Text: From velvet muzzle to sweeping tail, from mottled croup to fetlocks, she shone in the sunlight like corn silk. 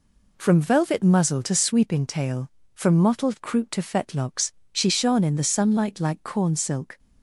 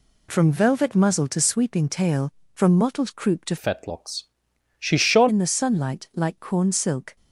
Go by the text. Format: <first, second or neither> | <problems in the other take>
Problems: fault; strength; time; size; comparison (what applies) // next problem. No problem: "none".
first | changes voice from "fetlocks" to "shone"; from 3.5 to 5.2 s; 1.7 s long